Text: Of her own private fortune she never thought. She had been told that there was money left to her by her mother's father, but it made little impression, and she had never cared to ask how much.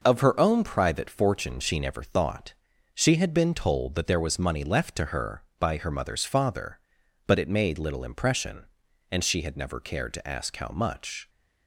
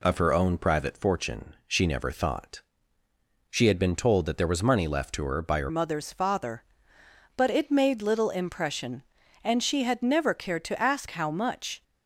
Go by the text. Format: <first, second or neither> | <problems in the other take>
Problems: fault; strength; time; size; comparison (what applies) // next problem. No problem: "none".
first | changes voice at "mother's"; from 5.6 s on; 6.2 s long